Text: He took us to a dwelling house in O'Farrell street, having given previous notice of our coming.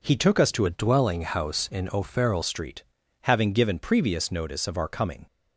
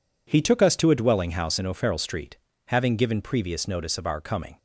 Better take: second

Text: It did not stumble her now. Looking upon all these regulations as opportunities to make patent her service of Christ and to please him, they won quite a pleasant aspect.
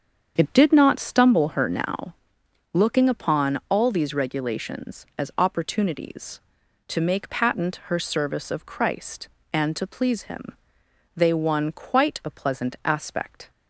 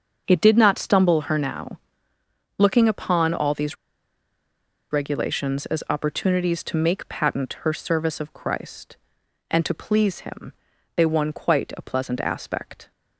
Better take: first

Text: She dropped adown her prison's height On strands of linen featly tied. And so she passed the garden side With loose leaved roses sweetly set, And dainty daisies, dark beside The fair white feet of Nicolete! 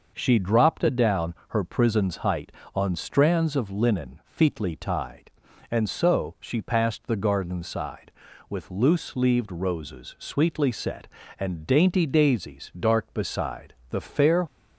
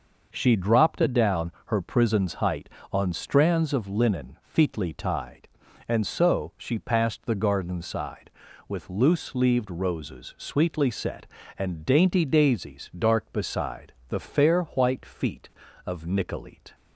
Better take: second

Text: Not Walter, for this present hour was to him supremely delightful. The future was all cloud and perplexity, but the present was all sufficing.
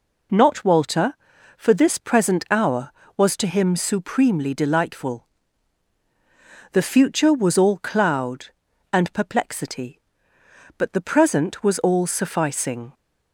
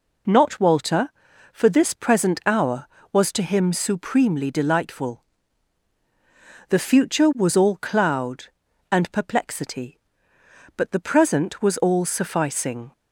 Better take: neither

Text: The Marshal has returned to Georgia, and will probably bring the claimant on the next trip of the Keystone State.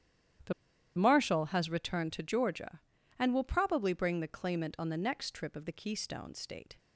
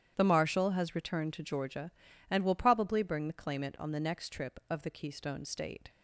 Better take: second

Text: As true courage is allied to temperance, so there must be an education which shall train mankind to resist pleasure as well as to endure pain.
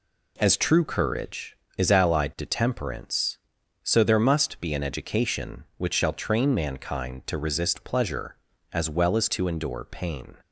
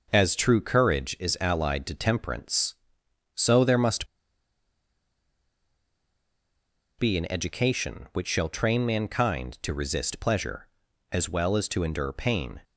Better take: first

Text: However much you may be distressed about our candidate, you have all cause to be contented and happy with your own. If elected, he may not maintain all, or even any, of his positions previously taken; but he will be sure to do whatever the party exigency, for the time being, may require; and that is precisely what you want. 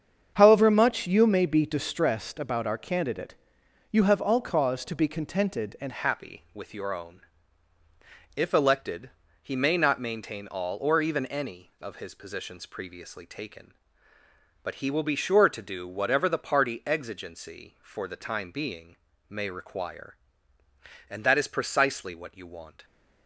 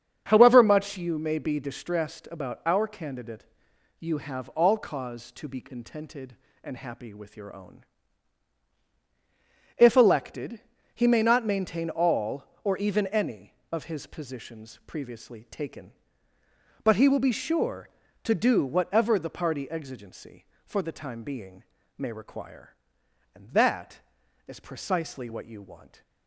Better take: second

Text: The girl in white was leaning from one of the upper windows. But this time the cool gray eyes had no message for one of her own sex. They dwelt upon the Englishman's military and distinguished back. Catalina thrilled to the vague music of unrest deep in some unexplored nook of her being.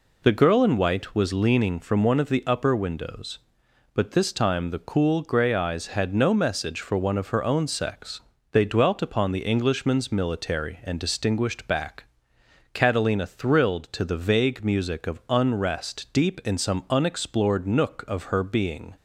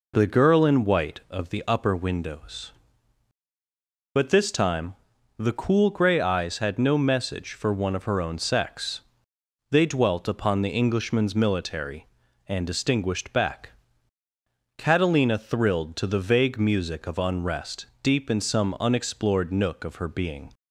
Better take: first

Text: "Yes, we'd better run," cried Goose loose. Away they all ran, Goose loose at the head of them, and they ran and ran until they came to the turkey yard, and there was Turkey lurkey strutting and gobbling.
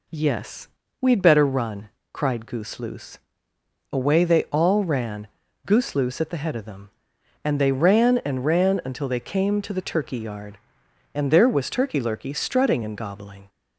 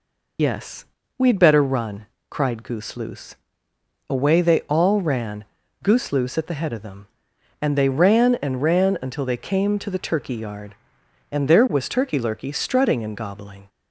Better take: first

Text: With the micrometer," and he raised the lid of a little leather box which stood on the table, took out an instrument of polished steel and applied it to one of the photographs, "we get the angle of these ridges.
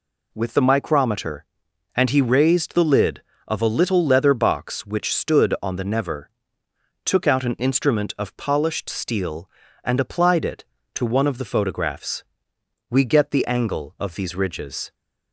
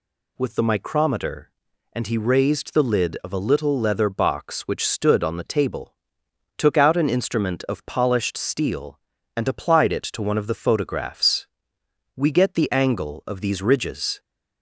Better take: second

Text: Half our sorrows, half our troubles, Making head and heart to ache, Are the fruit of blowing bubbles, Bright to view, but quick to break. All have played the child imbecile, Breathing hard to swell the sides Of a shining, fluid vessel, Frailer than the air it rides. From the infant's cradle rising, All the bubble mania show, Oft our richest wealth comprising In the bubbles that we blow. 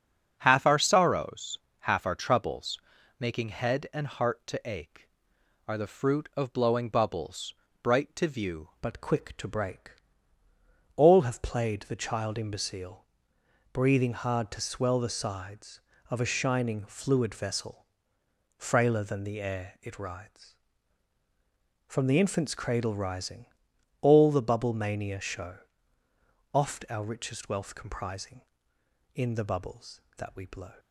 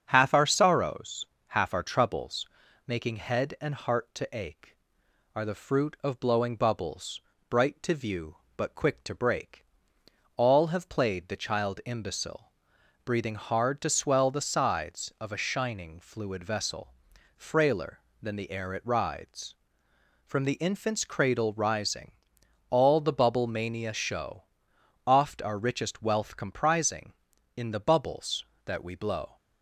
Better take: second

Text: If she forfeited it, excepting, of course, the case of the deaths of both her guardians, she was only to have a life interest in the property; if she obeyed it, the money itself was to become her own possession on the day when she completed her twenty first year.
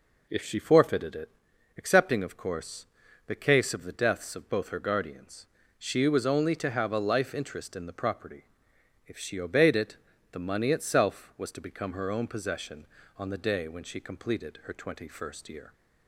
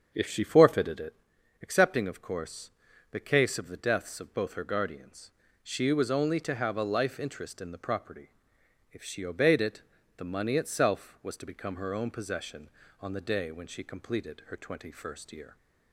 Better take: first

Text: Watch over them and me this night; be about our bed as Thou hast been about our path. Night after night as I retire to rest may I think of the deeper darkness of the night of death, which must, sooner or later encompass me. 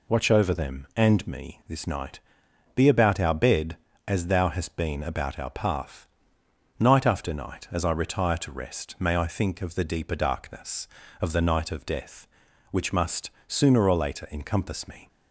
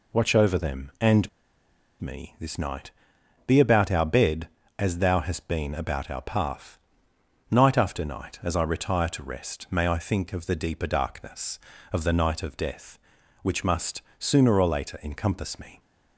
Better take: first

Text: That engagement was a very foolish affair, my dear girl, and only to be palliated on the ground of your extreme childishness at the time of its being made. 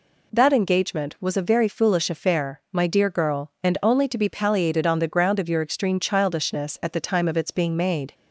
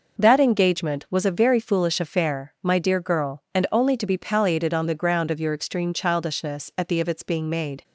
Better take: first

